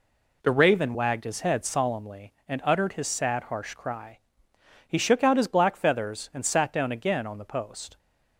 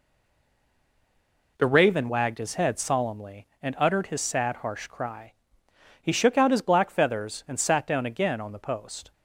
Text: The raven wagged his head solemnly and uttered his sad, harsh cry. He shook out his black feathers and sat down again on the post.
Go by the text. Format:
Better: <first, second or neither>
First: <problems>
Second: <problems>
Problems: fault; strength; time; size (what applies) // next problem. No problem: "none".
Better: first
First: none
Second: stays silent before the first word; noticeable; until 1.5 s; 1.5 s long